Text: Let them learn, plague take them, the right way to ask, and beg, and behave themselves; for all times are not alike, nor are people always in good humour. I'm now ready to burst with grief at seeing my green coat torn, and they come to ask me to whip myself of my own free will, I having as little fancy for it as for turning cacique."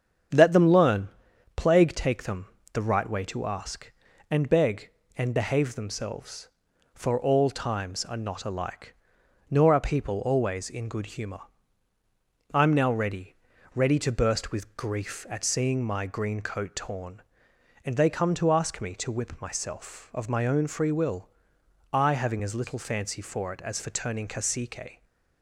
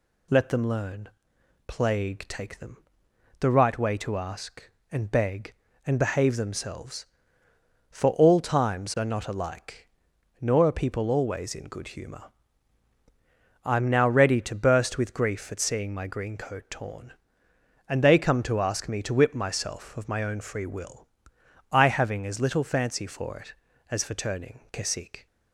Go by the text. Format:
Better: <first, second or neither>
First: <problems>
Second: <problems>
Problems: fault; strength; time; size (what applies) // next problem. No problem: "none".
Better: second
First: starts louder than the rest; strong; until 1.8 s; 8 dB // says "ready" twice; at 13.7 s // stays silent after the last word; slight; from 24.9 s on; 0.5 s long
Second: none